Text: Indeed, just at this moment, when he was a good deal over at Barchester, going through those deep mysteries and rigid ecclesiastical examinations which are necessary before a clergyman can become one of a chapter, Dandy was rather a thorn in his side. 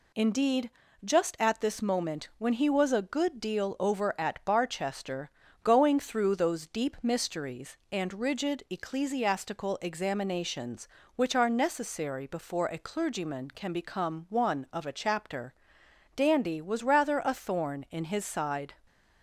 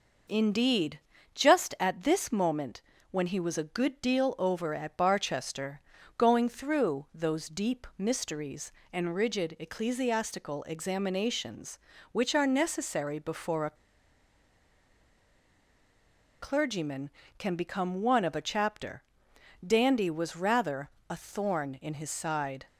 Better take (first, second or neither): first